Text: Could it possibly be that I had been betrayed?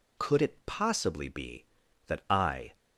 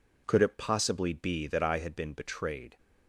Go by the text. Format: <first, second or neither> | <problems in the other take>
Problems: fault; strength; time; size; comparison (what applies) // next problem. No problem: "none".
second | stops before "had been betrayed"; at 2.7 s